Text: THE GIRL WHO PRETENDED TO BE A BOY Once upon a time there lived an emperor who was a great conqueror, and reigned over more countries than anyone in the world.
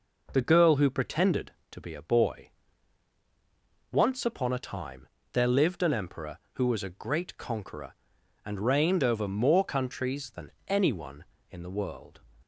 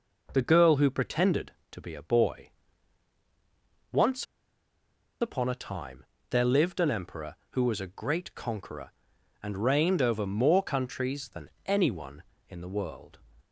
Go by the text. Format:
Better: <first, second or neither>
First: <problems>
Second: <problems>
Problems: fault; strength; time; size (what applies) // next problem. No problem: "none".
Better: first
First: pauses between "BOY" and "Once"; strong; at 2.5 s; 1.4 s long // pauses between "time" and "there"; slight; at 5.0 s; 0.26 s long // pauses between "than" and "anyone"; slight; at 10.5 s; 0.16 s long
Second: pauses between "BOY" and "Once"; strong; at 2.5 s; 1.4 s long // pauses between "Once" and "upon"; noticeable; at 4.2 s; 0.97 s long // pauses between "time" and "there"; slight; at 6.0 s; 0.26 s long // pauses between "than" and "anyone"; slight; at 11.5 s; 0.16 s long